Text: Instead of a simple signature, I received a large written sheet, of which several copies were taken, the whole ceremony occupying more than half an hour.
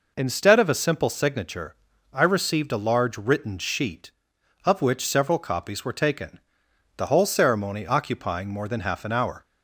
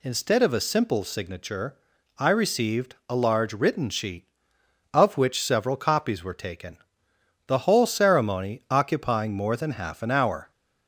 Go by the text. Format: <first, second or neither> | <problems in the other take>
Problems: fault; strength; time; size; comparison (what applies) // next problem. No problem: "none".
neither | none